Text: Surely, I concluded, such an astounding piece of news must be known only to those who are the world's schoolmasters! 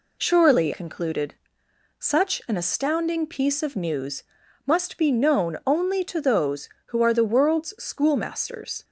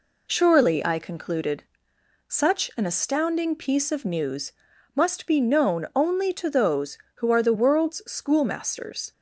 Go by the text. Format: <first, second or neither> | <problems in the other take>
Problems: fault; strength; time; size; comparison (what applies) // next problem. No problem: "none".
second | skips "I"; at 0.7 s // pauses between "news" and "must"; at 4.2 s; 0.42 s long; also in the second